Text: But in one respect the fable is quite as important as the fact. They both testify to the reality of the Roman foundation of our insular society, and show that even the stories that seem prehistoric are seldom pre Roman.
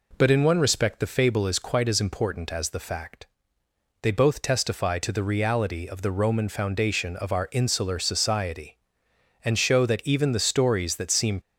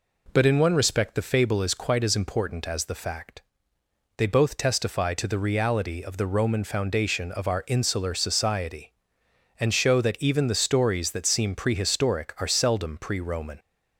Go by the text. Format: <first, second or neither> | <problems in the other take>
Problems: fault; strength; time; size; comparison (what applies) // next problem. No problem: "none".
second | stops before "prehistoric are seldom pre Roman"; at 11.4 s